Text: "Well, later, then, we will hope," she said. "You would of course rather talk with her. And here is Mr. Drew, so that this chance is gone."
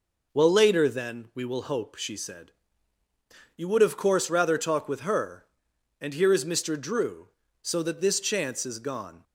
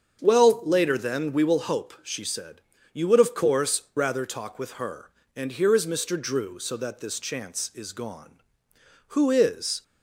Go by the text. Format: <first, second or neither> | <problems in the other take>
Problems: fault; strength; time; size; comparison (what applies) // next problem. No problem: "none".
first | starts louder than the rest; strong; until 1.2 s; 7 dB // goes on to say "Who is"; noticeable; from 9.1 s on; 0.68 s long